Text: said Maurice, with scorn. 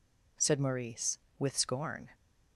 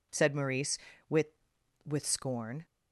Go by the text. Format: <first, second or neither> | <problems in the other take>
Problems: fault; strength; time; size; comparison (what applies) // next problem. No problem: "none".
first | says "with" twice; at 1.8 s